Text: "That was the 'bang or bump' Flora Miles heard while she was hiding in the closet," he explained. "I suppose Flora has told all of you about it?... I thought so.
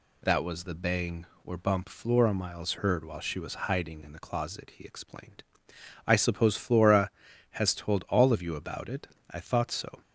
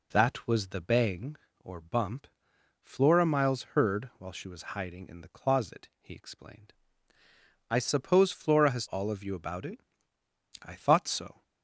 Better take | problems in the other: first | pauses between "bump" and "Flora"; noticeable; at 2.2 s; 0.54 s long // pauses between "Miles" and "heard"; slight; at 3.6 s; 0.18 s long // skips "told"; at 8.8 s

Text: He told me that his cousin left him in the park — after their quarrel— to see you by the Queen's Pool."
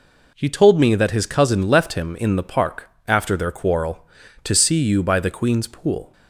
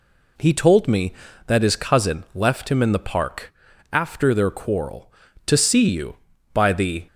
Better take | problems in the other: first | stops before "Queen's Pool"; at 7.0 s

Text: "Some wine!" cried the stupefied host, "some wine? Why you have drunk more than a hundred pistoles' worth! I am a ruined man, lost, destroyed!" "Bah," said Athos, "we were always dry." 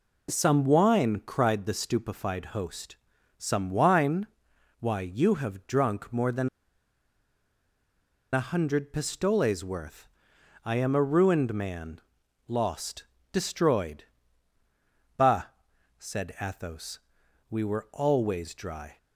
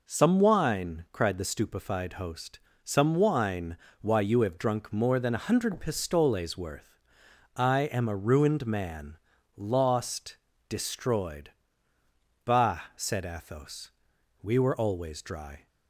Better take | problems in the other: second | pauses between "than" and "a"; strong; at 6.4 s; 1.8 s long

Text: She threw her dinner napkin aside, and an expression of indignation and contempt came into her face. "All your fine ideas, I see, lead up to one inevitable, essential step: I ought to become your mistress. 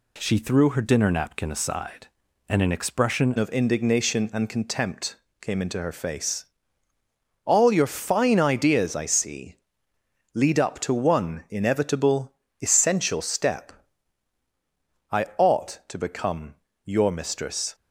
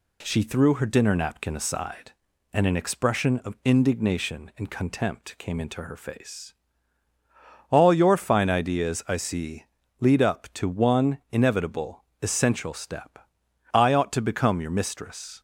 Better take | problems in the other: second | changes voice at "of"; from 3.3 s on; 14.4 s long // pauses between "contempt" and "came"; slight; at 5.1 s; 0.24 s long // pauses between "become" and "your"; slight; at 16.5 s; 0.30 s long

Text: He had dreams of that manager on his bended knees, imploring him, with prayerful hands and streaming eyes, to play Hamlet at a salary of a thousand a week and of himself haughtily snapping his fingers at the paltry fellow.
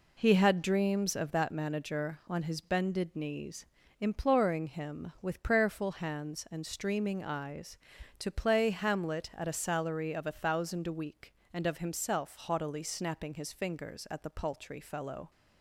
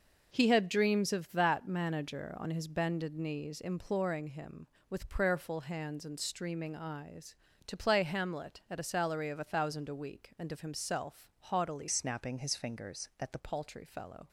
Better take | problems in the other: first | changes voice from "snapping" to "the"; from 11.8 to 13.3 s; 1.5 s long

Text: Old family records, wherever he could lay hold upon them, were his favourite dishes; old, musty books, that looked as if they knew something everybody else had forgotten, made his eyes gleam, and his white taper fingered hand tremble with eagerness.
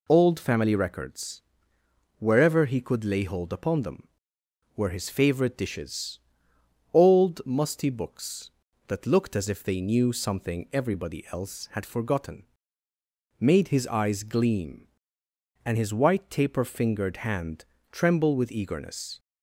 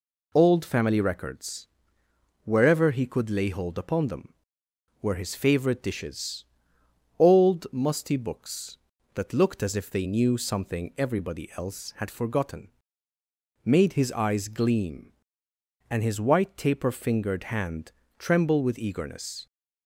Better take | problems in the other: neither | pauses between "hand" and "tremble"; slight; the same in both

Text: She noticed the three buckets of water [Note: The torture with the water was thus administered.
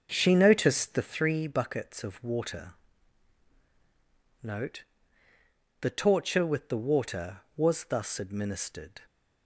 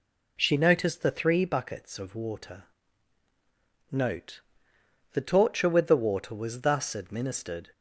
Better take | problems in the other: second | starts louder than the rest; noticeable; until 1.1 s; 6 dB // pauses between "water" and "Note"; strong; at 2.7 s; 1.6 s long; also in the second

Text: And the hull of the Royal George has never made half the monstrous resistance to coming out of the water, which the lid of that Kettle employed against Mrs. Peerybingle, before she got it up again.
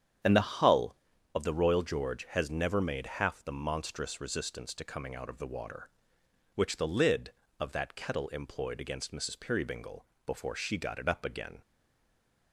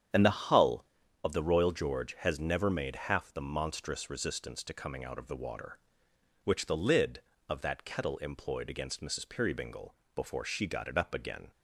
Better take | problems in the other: second | starts louder than the rest; strong; until 1.6 s; 8.5 dB; strong in the second // stays silent after the last word; slight; from 11.6 s on; 0.9 s long

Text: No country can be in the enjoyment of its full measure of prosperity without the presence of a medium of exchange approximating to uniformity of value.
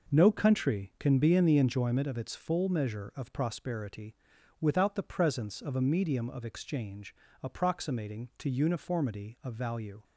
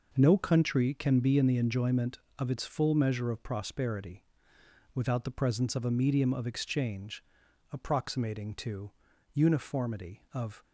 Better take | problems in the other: first | pauses between "prosperity" and "without"; noticeable; at 4.2 s; 0.72 s long; noticeable in the first // pauses between "exchange" and "approximating"; noticeable; at 7.2 s; 0.48 s long; slight in the first // pauses between "to" and "uniformity"; at 8.9 s; 0.42 s long // stops before "value"; at 10.6 s

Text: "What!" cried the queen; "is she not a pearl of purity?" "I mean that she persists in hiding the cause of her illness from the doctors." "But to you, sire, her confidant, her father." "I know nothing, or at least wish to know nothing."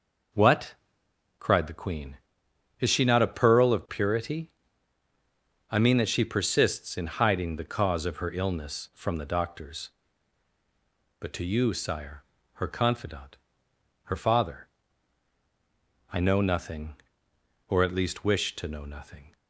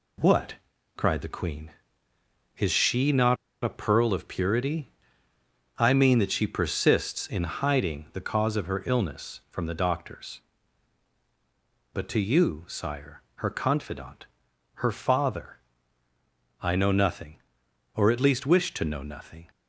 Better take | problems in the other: first | pauses between "not" and "a"; slight; at 3.3 s; 0.28 s long

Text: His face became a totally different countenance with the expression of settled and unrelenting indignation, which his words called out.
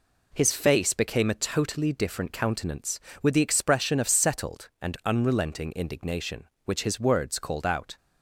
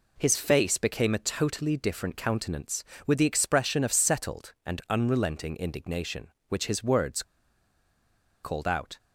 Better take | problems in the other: first | pauses between "words" and "called"; at 7.2 s; 1.2 s long

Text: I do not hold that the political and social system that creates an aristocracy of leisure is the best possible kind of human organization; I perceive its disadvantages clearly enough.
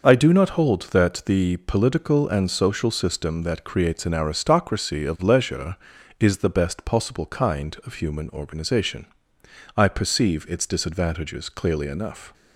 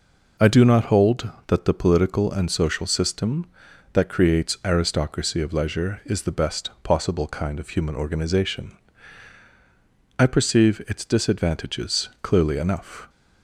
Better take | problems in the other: first | skips "an"; at 4.6 s

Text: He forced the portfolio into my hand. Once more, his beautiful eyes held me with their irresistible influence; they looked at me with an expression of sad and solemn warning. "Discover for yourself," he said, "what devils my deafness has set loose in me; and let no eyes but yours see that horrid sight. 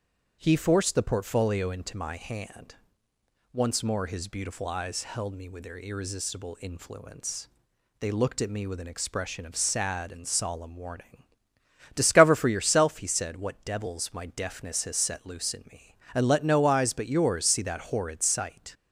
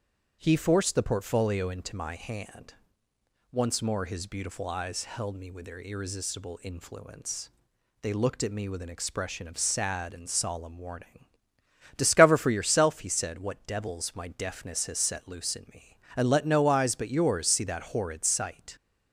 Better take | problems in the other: neither | starts louder than the rest; strong; the same in both

